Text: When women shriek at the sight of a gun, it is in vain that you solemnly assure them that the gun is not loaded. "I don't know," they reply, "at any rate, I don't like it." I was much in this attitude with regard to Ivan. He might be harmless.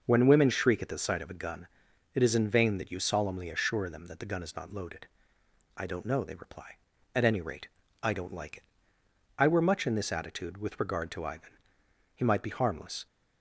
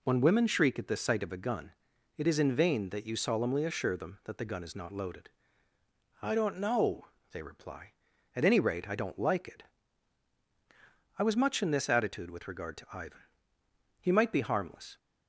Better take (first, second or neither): second